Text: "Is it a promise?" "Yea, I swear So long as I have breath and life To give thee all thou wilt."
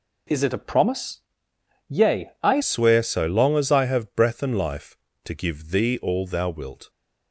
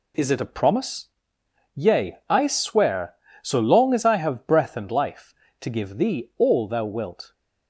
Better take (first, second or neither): second